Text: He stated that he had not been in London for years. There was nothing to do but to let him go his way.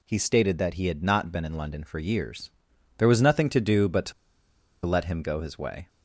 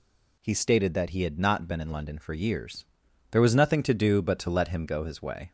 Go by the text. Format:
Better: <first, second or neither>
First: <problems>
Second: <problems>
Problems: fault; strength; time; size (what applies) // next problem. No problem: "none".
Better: second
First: pauses between "to" and "let"; noticeable; at 4.1 s; 0.72 s long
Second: none